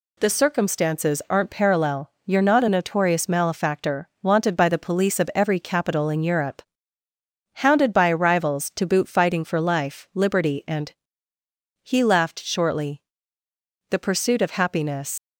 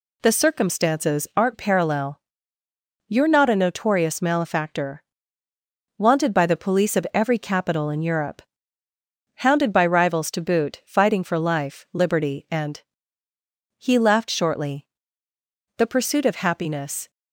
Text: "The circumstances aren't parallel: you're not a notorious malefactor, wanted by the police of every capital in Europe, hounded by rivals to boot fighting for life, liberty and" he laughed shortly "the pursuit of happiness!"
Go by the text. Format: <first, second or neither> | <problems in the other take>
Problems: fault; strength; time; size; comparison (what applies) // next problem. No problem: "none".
second | pauses between "and" and "he"; noticeable; at 10.9 s; 0.88 s long; noticeable in the second // pauses between "shortly" and "the"; noticeable; at 13.0 s; 0.88 s long; noticeable in the second // leaves "happiness" unfinished; at 15.1 s; 90 ms